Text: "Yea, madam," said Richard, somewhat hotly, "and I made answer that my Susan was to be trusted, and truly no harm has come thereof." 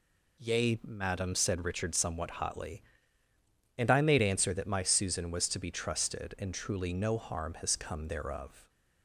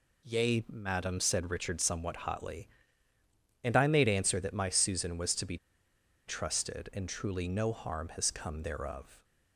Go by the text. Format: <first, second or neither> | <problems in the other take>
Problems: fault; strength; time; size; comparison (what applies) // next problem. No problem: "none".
first | pauses between "be" and "trusted"; noticeable; at 5.5 s; 0.70 s long